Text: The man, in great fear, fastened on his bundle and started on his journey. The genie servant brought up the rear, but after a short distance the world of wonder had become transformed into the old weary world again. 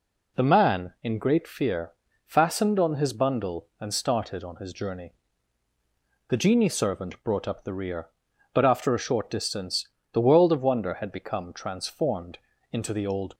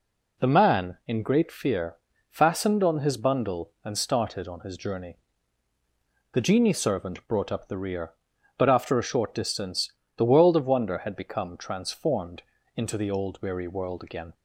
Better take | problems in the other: second | pauses between "distance" and "the"; slight; at 9.8 s; 0.24 s long; slight in the second // pauses between "transformed" and "into"; slight; at 12.3 s; 0.32 s long; slight in the second // stops before "weary world again"; at 13.3 s

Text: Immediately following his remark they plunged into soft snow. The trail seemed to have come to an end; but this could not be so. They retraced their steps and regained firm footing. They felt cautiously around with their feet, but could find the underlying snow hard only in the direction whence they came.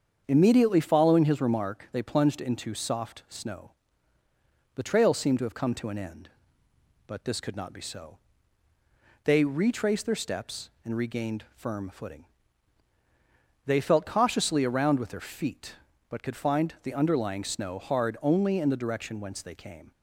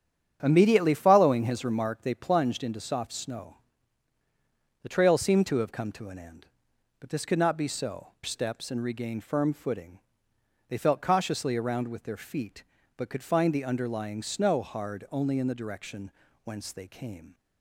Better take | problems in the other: first | starts louder than the rest; strong; until 1.4 s; 9 dB; strong in the first // skips "They retraced their"; at 8.1 s // pauses between "direction" and "whence"; slight; at 16.1 s; 0.32 s long

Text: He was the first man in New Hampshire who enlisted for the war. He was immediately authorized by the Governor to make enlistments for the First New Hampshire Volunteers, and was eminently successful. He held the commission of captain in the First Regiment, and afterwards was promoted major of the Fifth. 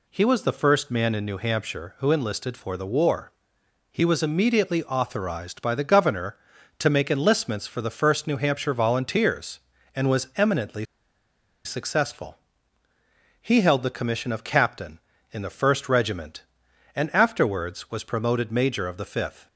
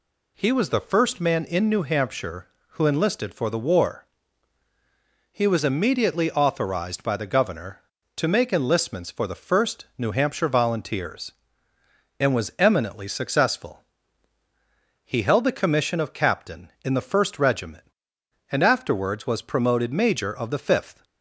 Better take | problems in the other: second | pauses between "eminently" and "successful"; noticeable; at 10.8 s; 0.79 s long

